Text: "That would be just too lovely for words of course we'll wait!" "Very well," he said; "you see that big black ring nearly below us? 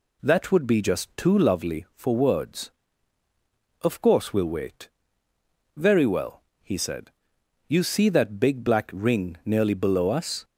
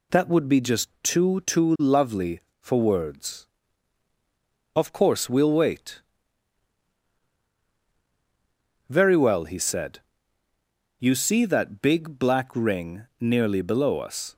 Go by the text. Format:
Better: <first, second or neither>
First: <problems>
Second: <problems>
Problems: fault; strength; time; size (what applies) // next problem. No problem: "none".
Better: first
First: none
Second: says "too" twice; at 1.4 s